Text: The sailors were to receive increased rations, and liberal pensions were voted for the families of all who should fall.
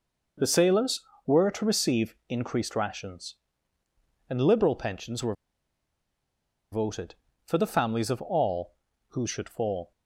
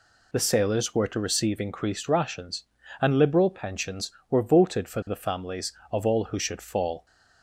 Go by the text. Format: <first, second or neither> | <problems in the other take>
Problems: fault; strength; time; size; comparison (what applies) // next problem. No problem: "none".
second | pauses between "were" and "voted"; strong; at 5.3 s; 1.3 s long